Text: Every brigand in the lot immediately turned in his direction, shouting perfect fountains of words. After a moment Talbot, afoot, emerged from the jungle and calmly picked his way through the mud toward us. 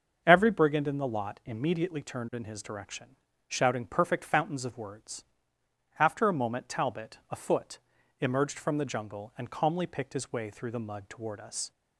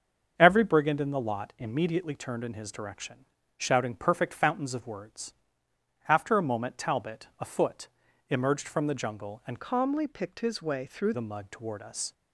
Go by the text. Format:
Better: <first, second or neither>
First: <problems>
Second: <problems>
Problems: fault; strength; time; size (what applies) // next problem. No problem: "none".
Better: first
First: starts louder than the rest; until 1.2 s; 6.5 dB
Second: starts louder than the rest; until 1.3 s; 6.5 dB // changes voice from "calmly" to "through"; from 9.6 to 11.1 s; 1.5 s long